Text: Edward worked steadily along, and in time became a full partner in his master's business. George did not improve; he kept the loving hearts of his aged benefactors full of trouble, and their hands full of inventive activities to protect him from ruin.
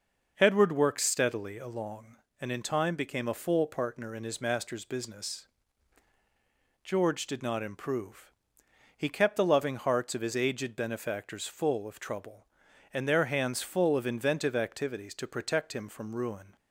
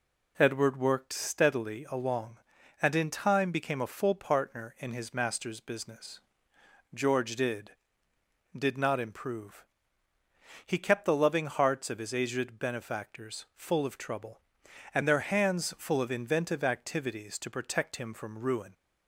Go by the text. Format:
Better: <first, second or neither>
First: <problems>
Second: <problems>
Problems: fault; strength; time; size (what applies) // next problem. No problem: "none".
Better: first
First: none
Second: says "did" twice; at 8.5 s